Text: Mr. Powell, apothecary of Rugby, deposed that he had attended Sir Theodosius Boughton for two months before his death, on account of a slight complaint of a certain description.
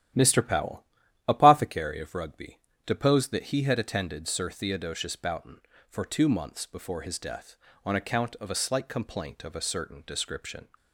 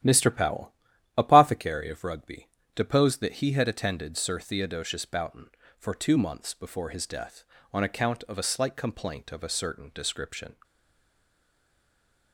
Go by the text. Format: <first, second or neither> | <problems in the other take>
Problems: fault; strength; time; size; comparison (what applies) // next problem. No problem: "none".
first | starts louder than the rest; strong; until 1.4 s; 12 dB; strong in the first // stays silent after the last word; noticeable; from 10.6 s on; 1.7 s long